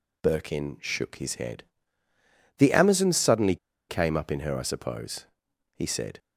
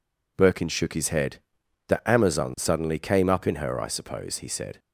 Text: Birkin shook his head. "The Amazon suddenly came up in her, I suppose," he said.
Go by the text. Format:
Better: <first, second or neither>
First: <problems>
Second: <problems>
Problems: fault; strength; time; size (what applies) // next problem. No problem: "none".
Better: second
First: pauses between "suddenly" and "came"; slight; at 3.5 s; 0.33 s long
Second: none